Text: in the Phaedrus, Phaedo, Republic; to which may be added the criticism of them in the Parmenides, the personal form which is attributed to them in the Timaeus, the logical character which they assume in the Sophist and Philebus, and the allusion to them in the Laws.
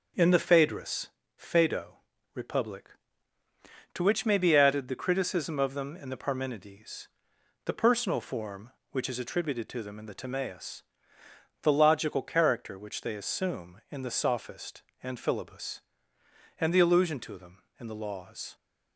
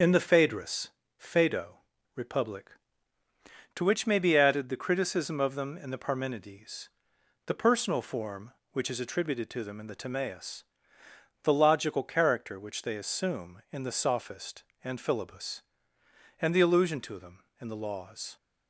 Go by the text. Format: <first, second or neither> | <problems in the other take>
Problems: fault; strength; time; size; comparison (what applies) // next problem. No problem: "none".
first | loses the start of "in"; at 0.0 s; 35 ms // starts louder than the rest; until 1.2 s; 6.5 dB; also in the first